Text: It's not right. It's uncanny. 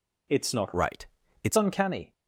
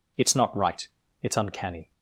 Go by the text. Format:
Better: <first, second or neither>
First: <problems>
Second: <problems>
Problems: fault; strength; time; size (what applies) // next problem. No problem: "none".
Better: second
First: changes voice from "right" to "It's"; from 0.7 to 1.5 s; 0.8 s long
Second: none